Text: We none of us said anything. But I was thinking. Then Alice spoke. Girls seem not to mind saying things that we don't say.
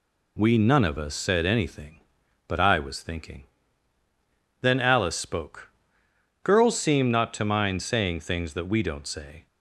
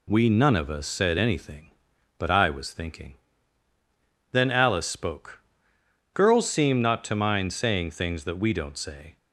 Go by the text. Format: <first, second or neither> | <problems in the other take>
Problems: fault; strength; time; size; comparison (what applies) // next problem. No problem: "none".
neither | none